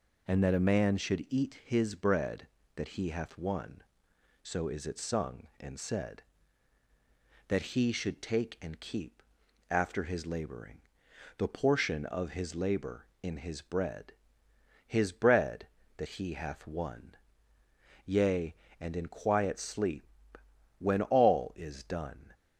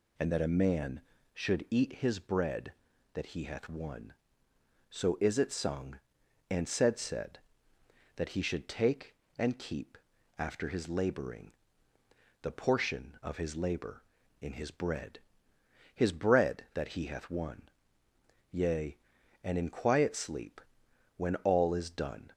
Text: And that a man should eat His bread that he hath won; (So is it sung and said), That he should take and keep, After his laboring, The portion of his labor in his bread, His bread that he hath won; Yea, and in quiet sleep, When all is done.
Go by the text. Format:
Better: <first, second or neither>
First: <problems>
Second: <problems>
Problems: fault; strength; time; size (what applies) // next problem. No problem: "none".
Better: first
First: none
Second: says "said" twice; at 7.0 s